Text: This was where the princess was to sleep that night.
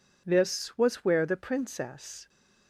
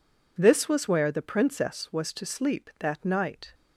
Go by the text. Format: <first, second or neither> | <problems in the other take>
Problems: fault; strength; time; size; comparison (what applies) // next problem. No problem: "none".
second | stops before "was to sleep that night"; at 2.2 s